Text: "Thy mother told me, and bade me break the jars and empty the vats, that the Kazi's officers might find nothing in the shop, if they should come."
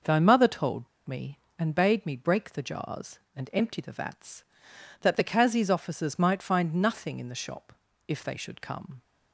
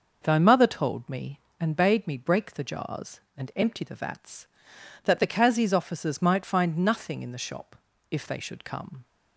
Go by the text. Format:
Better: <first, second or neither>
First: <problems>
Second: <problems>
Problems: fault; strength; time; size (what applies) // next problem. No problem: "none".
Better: second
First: pauses between "told" and "me"; slight; at 0.8 s; 0.19 s long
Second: none